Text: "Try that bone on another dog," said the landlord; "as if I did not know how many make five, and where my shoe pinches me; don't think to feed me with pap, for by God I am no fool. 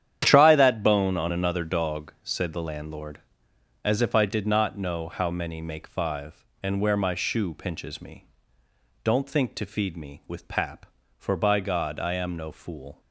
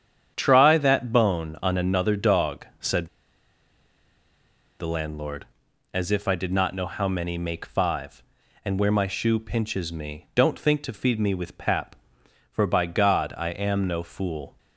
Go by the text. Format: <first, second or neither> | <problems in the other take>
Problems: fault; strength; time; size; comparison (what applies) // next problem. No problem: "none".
first | starts louder than the rest; strong; until 1.3 s; 8.5 dB; strong in the first // pauses between "said" and "the"; strong; at 3.0 s; 1.7 s long